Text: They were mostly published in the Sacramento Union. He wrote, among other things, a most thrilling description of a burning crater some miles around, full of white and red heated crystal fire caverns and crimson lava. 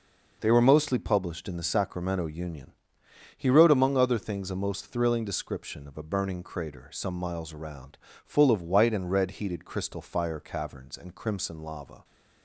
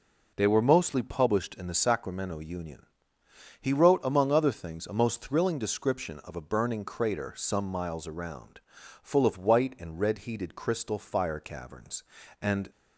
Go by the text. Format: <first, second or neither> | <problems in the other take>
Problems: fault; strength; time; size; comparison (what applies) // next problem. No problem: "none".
first | stops before "crimson lava"; at 12.7 s